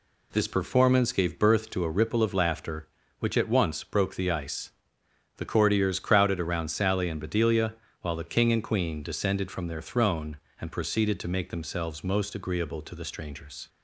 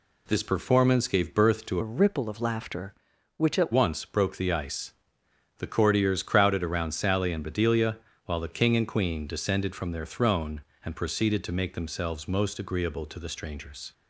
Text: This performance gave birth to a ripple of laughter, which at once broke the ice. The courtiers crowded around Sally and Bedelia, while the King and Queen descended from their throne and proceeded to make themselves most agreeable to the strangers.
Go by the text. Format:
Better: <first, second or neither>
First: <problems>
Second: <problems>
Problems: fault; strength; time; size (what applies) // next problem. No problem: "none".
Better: first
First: none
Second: changes voice from "a" to "at"; from 1.8 to 3.7 s; 1.9 s long